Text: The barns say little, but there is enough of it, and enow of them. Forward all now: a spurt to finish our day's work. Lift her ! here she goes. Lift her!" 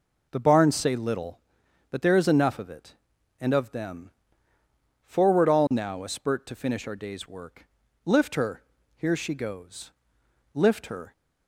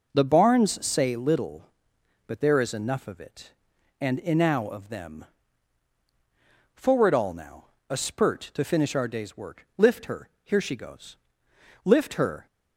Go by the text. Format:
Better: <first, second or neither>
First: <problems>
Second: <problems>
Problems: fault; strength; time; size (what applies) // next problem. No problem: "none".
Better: second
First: skips "enow"; at 3.5 s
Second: none